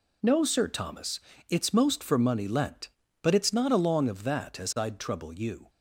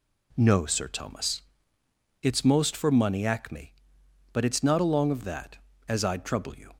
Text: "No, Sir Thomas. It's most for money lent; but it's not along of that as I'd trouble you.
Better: first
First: none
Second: says "acme" for "lent"; at 3.2 s

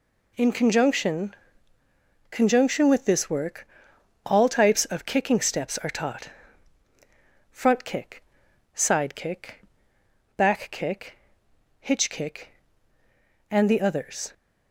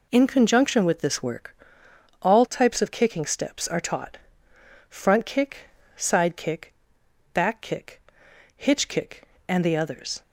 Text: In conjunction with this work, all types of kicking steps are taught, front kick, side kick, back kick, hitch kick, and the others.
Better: second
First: says "conjunction" twice; at 2.3 s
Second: none

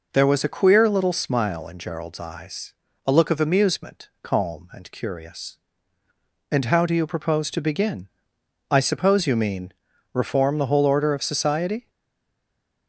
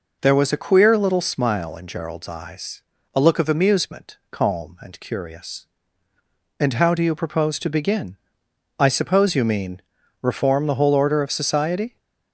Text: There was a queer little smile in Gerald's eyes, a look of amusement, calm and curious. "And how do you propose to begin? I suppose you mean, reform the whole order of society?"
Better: second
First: stays silent after the last word; from 11.8 s on; 1.0 s long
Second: none

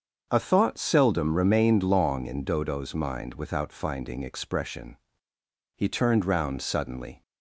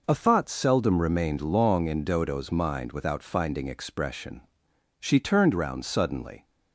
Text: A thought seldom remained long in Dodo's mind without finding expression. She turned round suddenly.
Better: second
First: starts louder than the rest; until 1.3 s; 7 dB // says "He" for "She"; at 5.7 s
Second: none

